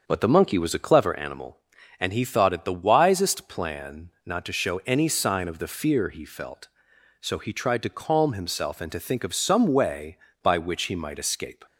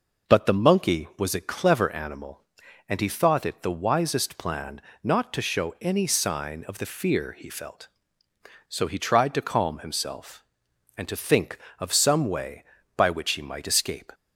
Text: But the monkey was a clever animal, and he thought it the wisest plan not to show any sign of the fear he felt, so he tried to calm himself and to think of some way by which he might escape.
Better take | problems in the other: second | starts louder than the rest; until 1.2 s; 6.5 dB // pauses between "plan" and "not"; slight; at 4.0 s; 0.16 s long; slight in the second

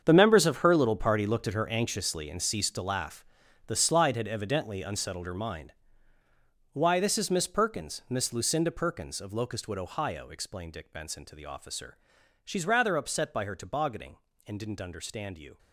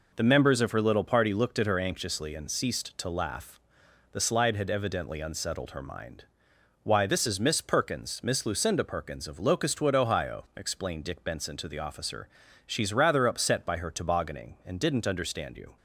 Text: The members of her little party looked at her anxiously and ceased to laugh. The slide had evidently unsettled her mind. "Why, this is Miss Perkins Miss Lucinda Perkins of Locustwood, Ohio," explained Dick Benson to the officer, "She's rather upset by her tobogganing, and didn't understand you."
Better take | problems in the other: second | gets quieter; strong; throughout; 13.5 dB

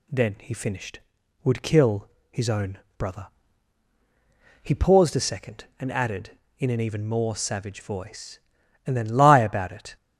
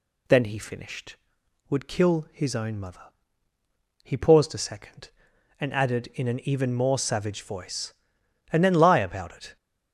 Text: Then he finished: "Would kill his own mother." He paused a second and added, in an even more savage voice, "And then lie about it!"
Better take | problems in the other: second | pauses between "kill" and "his"; slight; at 2.0 s; 0.22 s long // says "brother" for "mother"; at 2.9 s

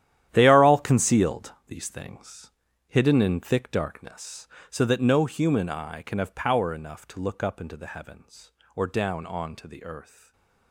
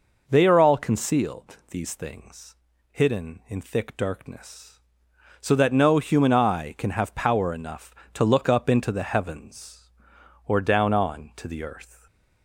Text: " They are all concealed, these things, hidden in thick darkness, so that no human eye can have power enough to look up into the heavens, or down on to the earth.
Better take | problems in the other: second | gets quieter; strong; throughout; 12 dB // stays silent after the last word; slight; from 10.0 s on; 0.7 s long

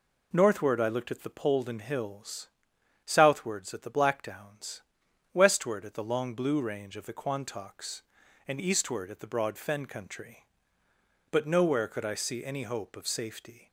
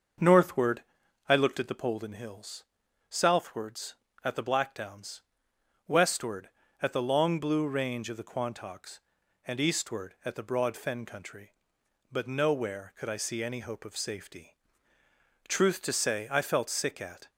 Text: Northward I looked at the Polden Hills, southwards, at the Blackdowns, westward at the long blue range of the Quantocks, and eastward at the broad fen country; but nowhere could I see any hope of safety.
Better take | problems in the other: first | starts louder than the rest; until 1.6 s; 6.5 dB // pauses between "Northward" and "I"; noticeable; at 0.8 s; 0.46 s long // goes on to say "Truth to say I felt sick at"; strong; from 15.4 s on; 1.8 s long

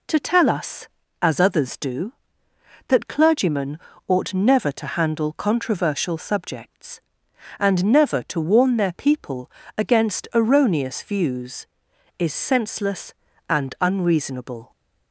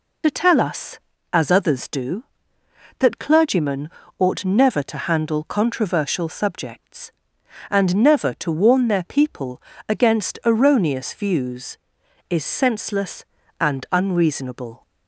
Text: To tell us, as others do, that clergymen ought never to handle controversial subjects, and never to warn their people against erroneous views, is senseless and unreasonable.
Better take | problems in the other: first | loses the start of "To"; at 0.2 s; 60 ms // pauses between "clergymen" and "ought"; slight; at 3.9 s; 0.28 s long; slight in the first // pauses between "people" and "against"; slight; at 9.6 s; 0.30 s long; slight in the first

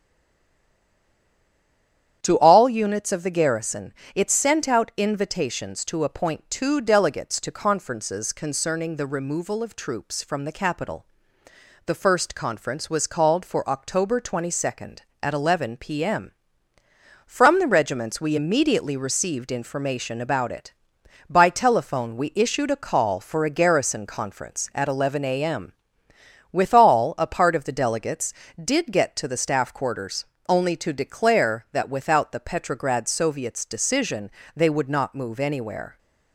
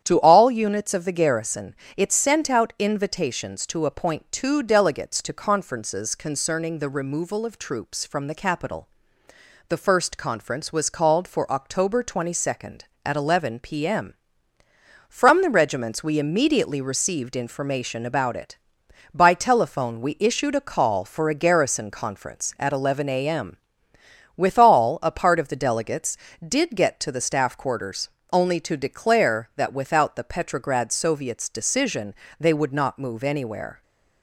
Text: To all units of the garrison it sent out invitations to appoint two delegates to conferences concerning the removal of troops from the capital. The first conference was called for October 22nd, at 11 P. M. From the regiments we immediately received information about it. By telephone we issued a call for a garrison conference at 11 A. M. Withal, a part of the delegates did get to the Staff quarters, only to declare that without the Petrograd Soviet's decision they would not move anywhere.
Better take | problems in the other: second | stays silent before the first word; until 2.2 s; 2.2 s long // starts louder than the rest; strong; until 3.2 s; 10 dB; strong in the second // pauses between "garrison" and "it"; slight; at 3.9 s; 0.20 s long; slight in the second // pauses between "M" and "Withal"; noticeable; at 25.7 s; 0.80 s long; noticeable in the second // pauses between "decision" and "they"; slight; at 34.2 s; 0.26 s long; slight in the second

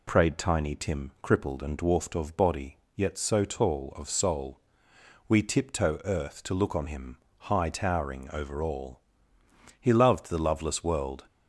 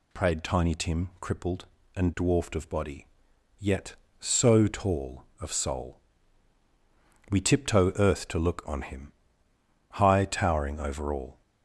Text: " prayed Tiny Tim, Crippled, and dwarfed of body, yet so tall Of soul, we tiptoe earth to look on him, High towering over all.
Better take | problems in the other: second | goes on to say "He loved the loveless world"; from 9.7 s on; 1.4 s long

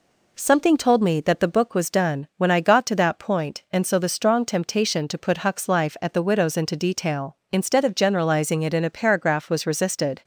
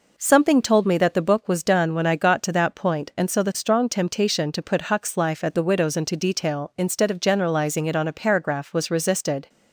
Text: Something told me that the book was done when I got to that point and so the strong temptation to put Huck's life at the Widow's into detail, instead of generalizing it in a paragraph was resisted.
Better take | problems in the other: first | says "on" for "in"; at 7.9 s

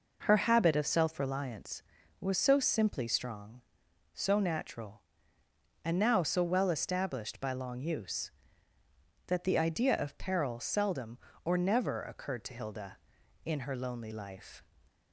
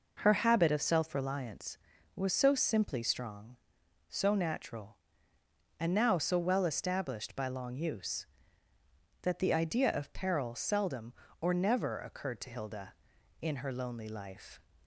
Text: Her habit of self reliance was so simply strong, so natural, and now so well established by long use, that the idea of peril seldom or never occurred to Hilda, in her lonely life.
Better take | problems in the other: neither | none

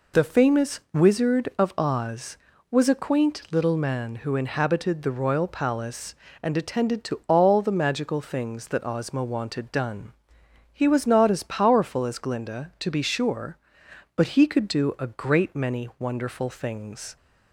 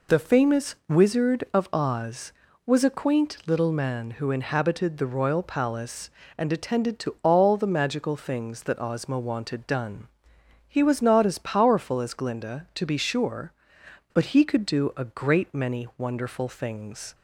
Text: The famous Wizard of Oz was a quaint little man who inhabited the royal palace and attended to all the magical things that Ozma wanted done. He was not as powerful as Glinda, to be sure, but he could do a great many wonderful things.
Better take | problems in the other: neither | none

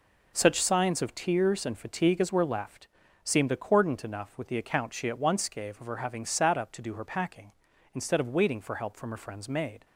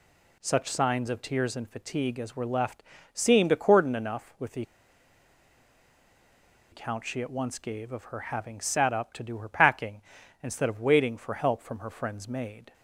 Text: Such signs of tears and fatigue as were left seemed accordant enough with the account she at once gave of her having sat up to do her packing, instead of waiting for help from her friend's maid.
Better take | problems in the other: first | pauses between "left" and "seemed"; slight; at 2.8 s; 0.30 s long; slight in the first // pauses between "the" and "account"; strong; at 4.6 s; 2.0 s long

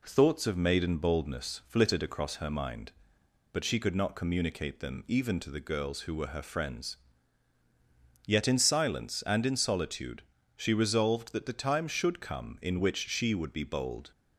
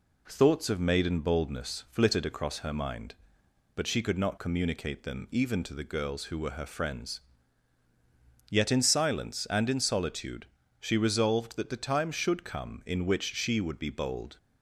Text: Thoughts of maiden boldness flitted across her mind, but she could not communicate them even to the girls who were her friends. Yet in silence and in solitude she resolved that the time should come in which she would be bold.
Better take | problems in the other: neither | pauses between "solitude" and "she"; slight; the same in both

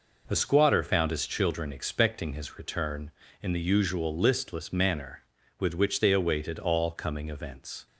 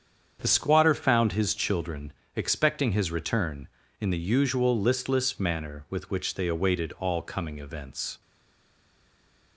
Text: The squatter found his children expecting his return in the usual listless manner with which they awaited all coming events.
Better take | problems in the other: first | starts louder than the rest; strong; until 1.4 s; 7.5 dB // pauses between "children" and "expecting"; slight; at 2.1 s; 0.20 s long // stays silent after the last word; noticeable; from 8.2 s on; 1.3 s long

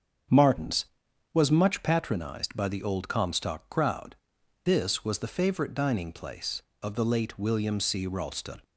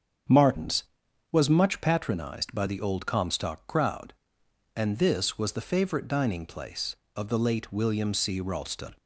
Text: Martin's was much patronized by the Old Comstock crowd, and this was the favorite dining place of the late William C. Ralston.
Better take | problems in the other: second | starts louder than the rest; strong; until 1.8 s; 7 dB; strong in the second // skips "and"; at 4.3 s

